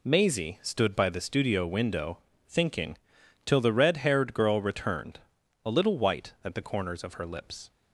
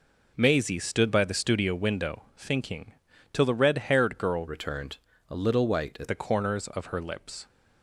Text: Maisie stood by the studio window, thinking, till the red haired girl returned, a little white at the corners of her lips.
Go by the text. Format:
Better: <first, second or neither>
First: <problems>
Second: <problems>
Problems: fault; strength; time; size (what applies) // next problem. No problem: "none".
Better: first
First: none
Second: changes voice from "returned" to "at"; from 4.4 to 6.0 s; 1.6 s long